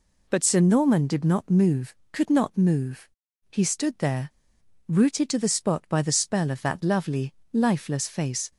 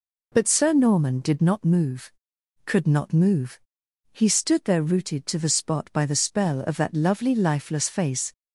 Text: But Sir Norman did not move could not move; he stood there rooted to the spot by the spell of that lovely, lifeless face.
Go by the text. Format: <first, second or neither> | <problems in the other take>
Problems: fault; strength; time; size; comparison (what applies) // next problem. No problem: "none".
second | pauses between "there" and "rooted"; noticeable; at 4.3 s; 0.57 s long